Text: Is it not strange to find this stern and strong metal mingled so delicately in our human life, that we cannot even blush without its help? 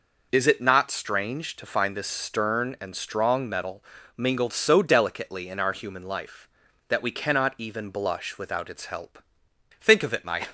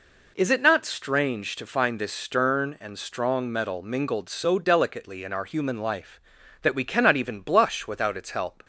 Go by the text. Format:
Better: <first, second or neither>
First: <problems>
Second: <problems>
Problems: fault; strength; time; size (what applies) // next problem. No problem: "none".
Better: second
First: pauses between "metal" and "mingled"; slight; at 3.8 s; 0.34 s long // goes on to say "Think of it my"; noticeable; from 9.7 s on; 0.70 s long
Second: none